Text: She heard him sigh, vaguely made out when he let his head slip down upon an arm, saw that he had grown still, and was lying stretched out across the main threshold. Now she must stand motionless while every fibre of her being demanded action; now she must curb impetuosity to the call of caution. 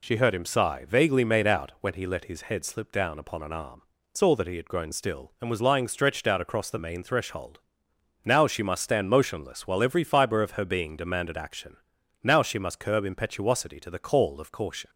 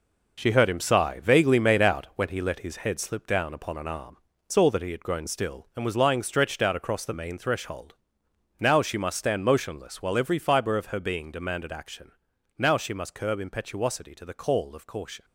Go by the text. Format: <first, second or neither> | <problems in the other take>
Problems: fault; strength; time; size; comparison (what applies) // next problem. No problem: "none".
first | gets quieter; strong; throughout; 9 dB